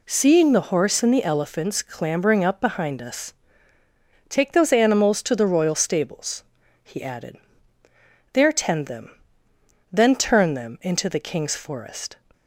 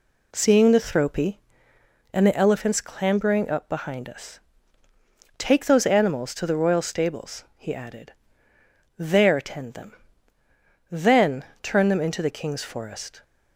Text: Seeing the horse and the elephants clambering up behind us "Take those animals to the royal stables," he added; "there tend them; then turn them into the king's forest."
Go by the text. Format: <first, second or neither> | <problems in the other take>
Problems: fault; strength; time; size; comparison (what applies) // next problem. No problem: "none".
first | says "thropy" for "horse"; at 0.8 s // pauses between "us" and "Take"; at 4.3 s; 1.0 s long; noticeable in the first // pauses between "then" and "turn"; slight; at 11.4 s; 0.18 s long